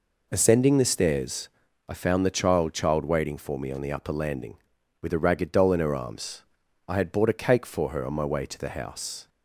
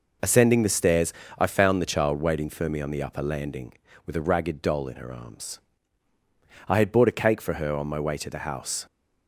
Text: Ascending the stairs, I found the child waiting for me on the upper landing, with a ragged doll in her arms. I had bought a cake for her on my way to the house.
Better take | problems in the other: second | says "child" twice; at 2.7 s

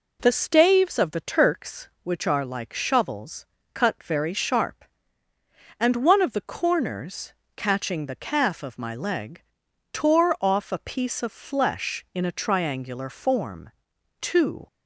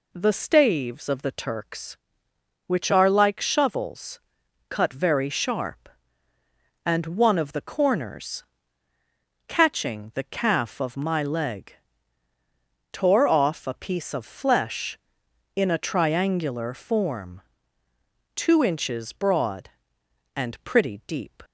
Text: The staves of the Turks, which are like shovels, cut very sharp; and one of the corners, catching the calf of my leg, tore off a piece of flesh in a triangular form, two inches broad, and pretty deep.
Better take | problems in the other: second | stops before "inches broad and pretty deep"; at 14.6 s

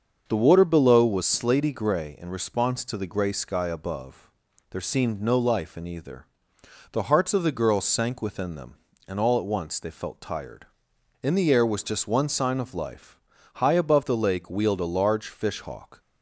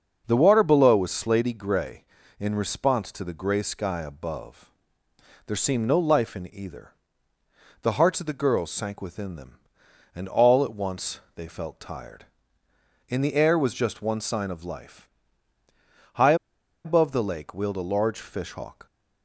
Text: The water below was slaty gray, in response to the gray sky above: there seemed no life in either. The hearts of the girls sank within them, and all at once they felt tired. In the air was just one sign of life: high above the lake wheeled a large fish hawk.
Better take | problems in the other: first | starts louder than the rest; until 1.2 s; 6 dB; also in the first // pauses between "once" and "they"; slight; at 11.1 s; 0.16 s long // pauses between "high" and "above"; noticeable; at 16.3 s; 0.50 s long

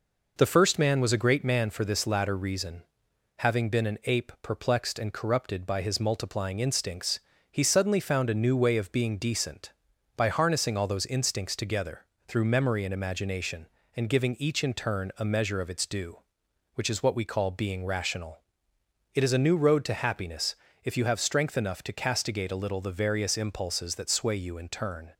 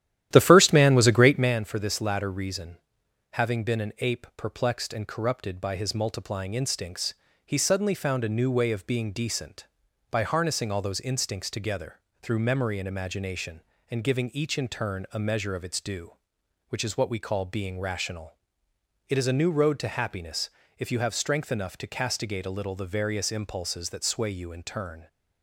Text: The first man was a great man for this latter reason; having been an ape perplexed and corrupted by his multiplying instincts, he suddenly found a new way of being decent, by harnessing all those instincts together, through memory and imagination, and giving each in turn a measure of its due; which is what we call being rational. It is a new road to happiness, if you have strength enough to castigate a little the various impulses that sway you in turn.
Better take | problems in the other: first | starts louder than the rest; strong; until 1.5 s; 12 dB

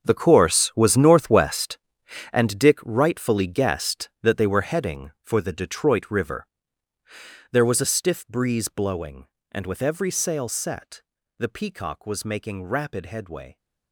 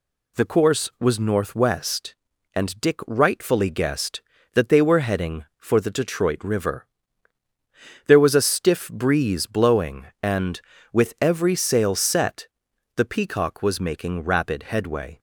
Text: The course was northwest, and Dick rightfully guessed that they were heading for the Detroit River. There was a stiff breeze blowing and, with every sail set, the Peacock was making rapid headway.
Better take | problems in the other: second | gets quieter; strong; throughout; 14.5 dB

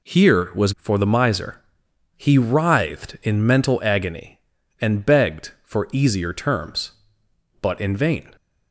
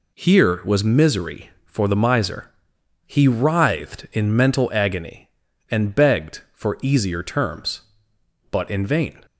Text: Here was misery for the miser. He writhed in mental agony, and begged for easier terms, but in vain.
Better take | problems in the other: second | skips "misery"; at 0.7 s

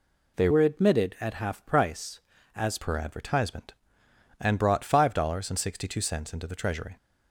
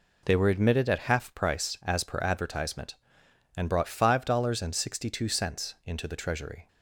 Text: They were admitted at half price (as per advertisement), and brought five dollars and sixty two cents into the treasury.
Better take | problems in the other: second | changes voice from "were" to "as"; from 0.4 to 2.7 s; 2.3 s long

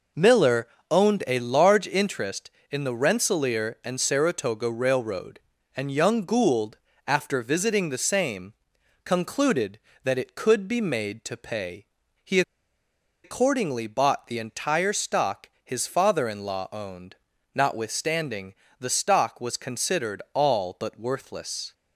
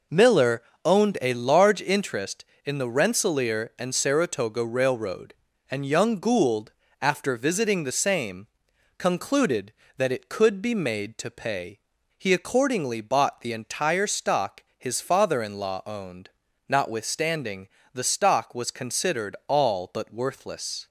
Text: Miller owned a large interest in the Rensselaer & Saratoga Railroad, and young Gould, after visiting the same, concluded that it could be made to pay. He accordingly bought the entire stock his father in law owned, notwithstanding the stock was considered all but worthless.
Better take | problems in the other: second | pauses between "Miller" and "owned"; slight; at 0.6 s; 0.22 s long; slight in the second // pauses between "He" and "accordingly"; noticeable; at 12.4 s; 0.82 s long // pauses between "notwithstanding" and "the"; slight; at 18.5 s; 0.26 s long; slight in the second

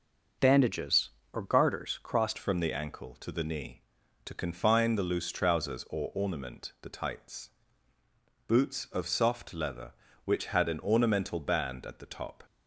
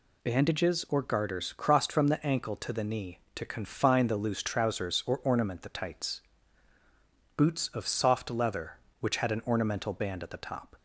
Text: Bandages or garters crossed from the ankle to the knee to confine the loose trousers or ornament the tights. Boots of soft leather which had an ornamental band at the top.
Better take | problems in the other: second | changes voice at "from"; from 2.3 s on; 10.1 s long

